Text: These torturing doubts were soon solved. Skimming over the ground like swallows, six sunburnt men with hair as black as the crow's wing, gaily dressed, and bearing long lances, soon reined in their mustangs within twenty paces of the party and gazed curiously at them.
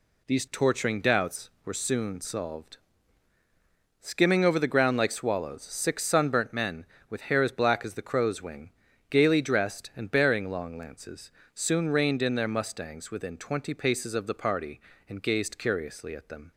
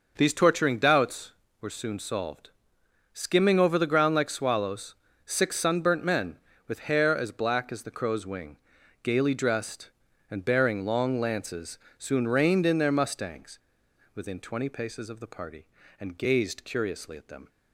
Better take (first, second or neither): first